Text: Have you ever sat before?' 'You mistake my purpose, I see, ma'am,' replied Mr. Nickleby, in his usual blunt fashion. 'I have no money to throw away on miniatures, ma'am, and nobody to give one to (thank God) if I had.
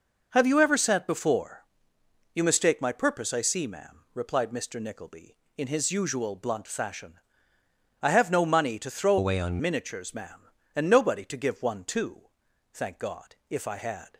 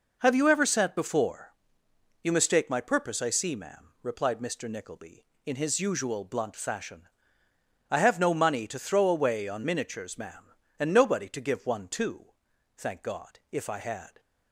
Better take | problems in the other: second | changes voice from "away" to "on"; from 9.1 to 9.5 s; 0.4 s long

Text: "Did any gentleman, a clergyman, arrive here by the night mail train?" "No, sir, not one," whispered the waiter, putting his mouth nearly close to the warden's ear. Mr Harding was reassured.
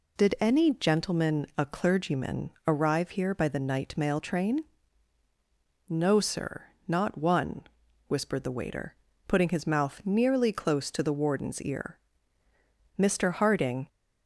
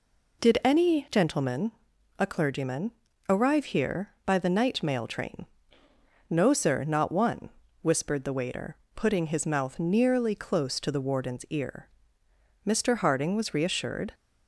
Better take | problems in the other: second | stops before "was reassured"; at 13.8 s

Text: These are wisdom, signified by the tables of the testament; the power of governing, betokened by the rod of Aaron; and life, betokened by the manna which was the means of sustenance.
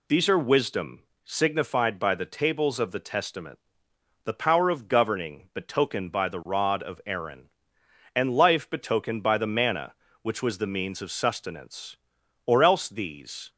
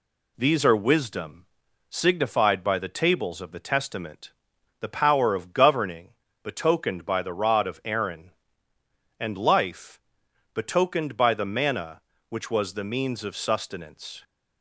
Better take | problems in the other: second | goes on to say "Or else these"; noticeable; from 12.4 s on; 1.0 s long

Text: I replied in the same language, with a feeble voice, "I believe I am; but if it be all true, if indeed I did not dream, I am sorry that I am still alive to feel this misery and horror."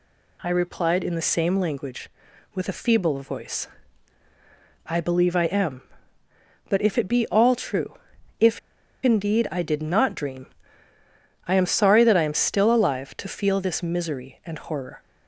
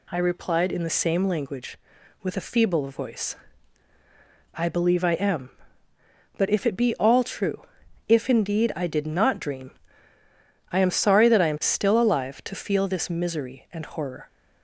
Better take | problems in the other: second | pauses between "if" and "indeed"; at 8.5 s; 0.44 s long

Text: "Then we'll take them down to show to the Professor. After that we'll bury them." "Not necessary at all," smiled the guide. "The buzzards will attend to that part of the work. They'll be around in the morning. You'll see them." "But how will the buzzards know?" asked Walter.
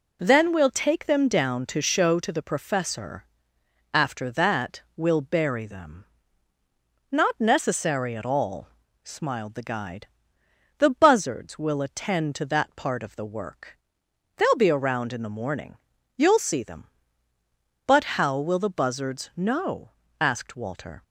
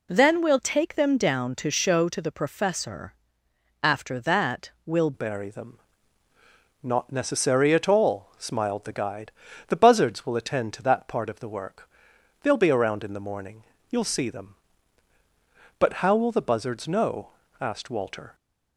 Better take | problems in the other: first | changes voice at "bury"; from 5.1 s on; 13.2 s long

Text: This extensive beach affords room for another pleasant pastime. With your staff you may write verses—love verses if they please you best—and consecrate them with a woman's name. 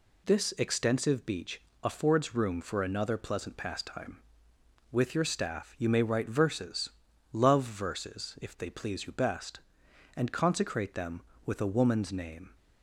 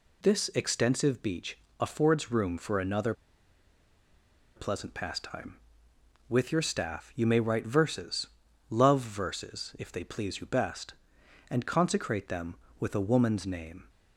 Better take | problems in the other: first | pauses between "beach" and "affords"; slight; at 1.5 s; 0.20 s long; slight in the first // pauses between "another" and "pleasant"; strong; at 3.1 s; 1.4 s long

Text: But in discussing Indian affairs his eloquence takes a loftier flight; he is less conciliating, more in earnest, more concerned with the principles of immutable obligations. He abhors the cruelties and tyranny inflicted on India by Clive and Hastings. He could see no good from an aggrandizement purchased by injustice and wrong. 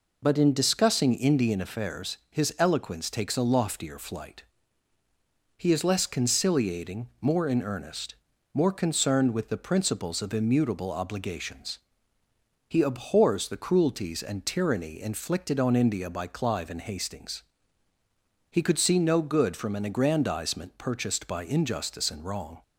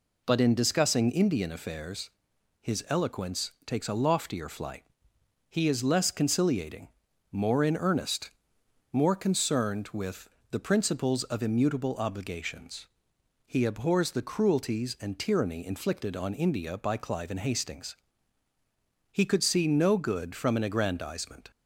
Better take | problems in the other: first | pauses between "affairs" and "his"; noticeable; at 2.0 s; 0.54 s long // pauses between "with" and "the"; slight; at 10.2 s; 0.22 s long // stops before "purchased by injustice and wrong"; at 21.5 s

